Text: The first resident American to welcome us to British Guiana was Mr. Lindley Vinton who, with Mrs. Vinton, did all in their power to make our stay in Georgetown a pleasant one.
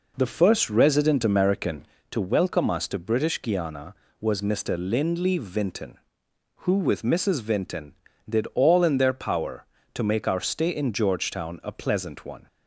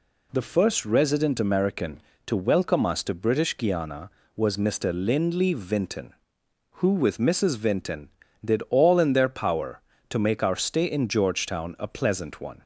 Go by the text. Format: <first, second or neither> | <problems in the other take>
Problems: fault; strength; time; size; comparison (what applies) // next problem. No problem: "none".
second | starts louder than the rest; noticeable; until 2.0 s; 4.5 dB